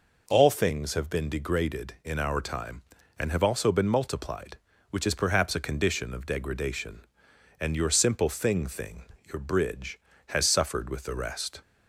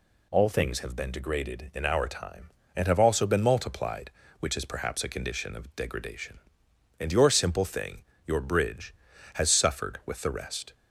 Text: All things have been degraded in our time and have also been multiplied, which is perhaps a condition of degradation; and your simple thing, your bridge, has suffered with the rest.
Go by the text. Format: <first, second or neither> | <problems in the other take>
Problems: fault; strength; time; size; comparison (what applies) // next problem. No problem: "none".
second | says "thing" twice; at 8.6 s